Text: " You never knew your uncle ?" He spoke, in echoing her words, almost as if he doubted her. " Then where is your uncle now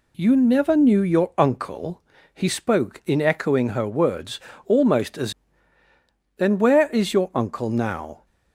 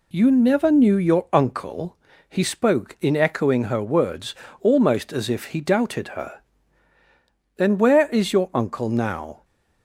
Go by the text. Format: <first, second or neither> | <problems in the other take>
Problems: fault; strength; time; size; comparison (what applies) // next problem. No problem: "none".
second | skips "if he doubted her"; at 5.5 s